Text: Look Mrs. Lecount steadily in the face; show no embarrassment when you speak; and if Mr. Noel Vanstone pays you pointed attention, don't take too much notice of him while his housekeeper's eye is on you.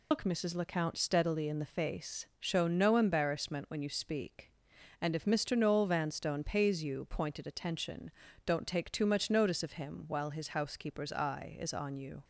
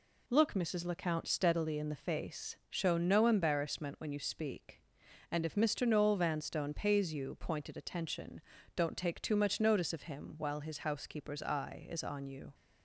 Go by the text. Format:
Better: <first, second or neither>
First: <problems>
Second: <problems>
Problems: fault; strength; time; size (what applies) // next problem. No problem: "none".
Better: second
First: loses the start of "Look"; at 0.1 s; 130 ms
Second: none